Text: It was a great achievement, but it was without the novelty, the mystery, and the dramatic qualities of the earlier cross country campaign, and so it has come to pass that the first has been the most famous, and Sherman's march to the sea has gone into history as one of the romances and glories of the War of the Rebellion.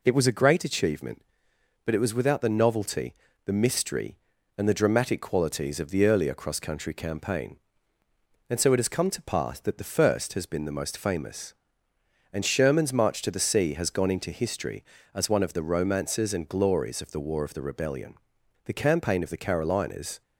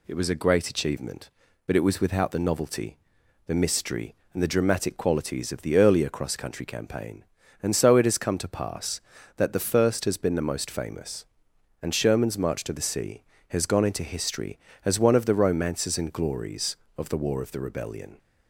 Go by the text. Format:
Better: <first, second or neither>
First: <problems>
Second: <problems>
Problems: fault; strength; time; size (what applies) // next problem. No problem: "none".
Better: second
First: goes on to say "The campaign of the Carolinas"; from 18.6 s on; 1.5 s long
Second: none